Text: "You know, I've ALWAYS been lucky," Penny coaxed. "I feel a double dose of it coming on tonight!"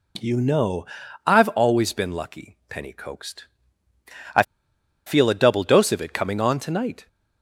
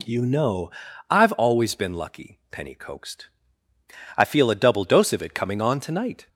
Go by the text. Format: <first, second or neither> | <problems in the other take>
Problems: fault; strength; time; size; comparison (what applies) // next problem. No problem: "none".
second | pauses between "I" and "feel"; noticeable; at 4.4 s; 0.63 s long